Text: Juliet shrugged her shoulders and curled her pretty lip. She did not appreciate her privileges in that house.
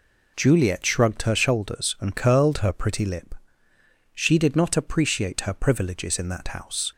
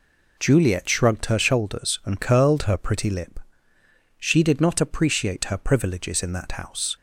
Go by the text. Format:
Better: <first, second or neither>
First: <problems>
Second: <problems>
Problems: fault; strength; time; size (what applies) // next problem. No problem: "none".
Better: neither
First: none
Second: none